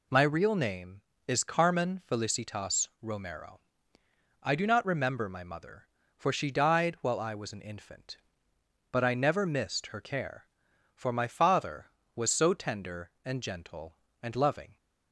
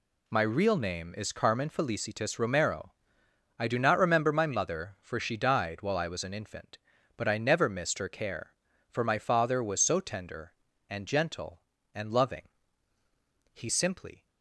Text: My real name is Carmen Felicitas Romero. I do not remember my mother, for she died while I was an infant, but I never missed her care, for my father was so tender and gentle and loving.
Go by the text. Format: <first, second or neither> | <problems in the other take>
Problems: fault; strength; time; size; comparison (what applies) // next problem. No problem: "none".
first | goes on to say "He simply"; noticeable; from 13.5 s on; 0.73 s long